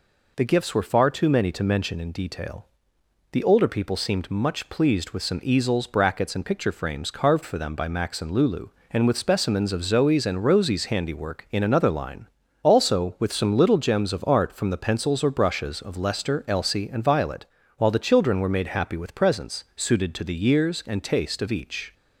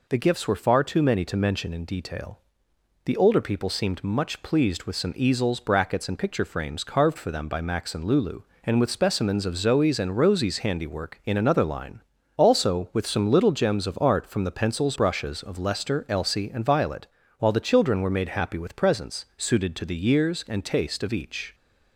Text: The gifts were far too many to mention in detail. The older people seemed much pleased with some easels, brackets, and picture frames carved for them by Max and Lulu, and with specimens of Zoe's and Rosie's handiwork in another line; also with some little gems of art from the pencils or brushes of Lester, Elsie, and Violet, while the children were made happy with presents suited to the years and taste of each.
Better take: first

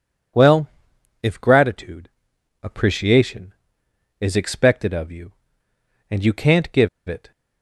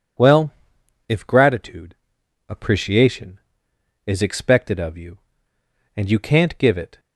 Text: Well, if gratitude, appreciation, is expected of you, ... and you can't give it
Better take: second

